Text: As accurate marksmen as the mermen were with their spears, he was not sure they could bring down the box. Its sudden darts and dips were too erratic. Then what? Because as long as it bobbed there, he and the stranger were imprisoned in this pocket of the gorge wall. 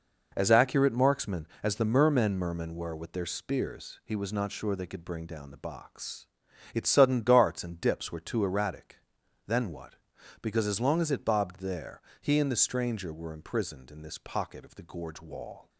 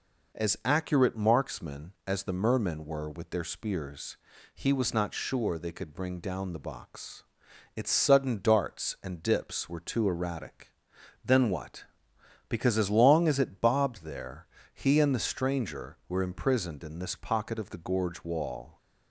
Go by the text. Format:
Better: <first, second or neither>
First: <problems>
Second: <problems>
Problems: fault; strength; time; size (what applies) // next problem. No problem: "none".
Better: second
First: says "mermen" twice; at 2.3 s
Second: none